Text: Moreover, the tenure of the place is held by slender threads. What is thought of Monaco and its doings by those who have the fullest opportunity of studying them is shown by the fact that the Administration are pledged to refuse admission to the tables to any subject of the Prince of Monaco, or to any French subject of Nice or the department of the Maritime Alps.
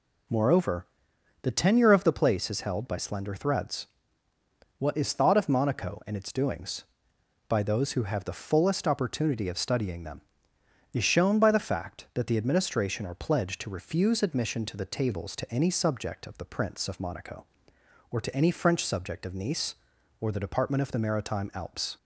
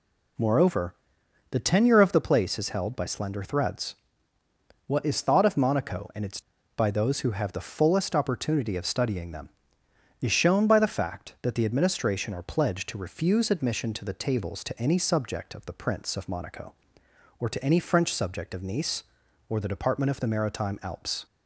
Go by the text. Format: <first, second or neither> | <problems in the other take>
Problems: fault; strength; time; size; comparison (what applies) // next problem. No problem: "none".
first | skips "doings"; at 6.5 s